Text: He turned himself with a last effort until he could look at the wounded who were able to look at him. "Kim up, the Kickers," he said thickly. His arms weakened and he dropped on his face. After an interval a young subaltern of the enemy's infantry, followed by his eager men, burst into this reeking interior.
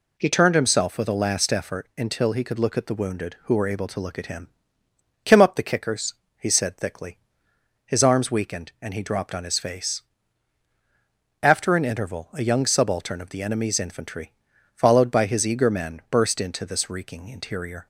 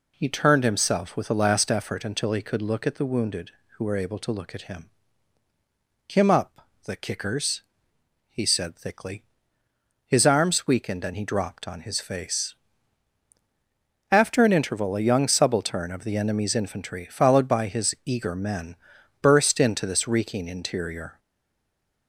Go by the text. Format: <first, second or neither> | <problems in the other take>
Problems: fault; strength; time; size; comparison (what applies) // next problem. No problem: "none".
first | stays silent after the last word; slight; from 21.1 s on; 0.9 s long